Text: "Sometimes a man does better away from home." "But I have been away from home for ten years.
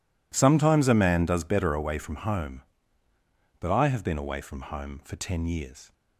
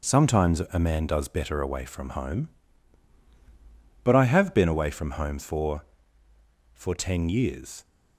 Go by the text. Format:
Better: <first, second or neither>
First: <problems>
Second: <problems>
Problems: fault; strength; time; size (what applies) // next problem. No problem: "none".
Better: first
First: none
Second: says "for" twice; at 6.7 s